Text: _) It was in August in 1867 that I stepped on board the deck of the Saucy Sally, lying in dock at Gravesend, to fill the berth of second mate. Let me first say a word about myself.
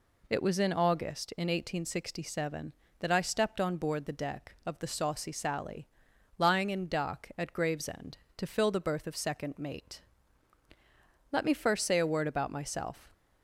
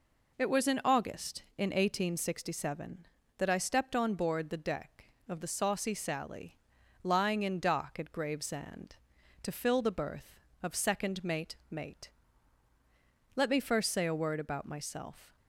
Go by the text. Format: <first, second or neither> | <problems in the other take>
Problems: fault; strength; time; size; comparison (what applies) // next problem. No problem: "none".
first | says "mate" twice; at 11.7 s